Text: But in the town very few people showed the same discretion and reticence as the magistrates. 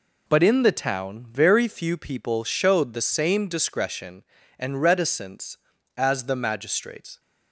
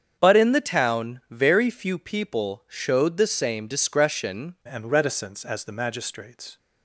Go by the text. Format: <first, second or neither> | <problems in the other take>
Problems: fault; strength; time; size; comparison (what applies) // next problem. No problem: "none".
first | starts louder than the rest; strong; until 1.2 s; 7.5 dB // changes voice at "and"; from 4.6 s on; 1.9 s long